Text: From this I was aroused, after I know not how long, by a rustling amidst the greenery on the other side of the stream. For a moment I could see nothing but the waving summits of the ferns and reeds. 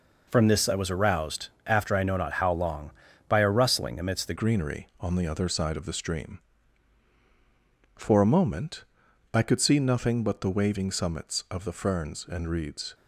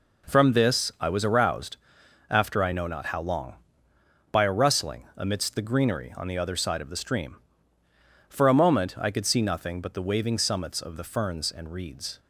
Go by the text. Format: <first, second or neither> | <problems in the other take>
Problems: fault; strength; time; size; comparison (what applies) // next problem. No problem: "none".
second | changes voice at "greenery"; from 4.3 s on; 8.6 s long // pauses between "moment" and "I"; noticeable; at 8.8 s; 0.50 s long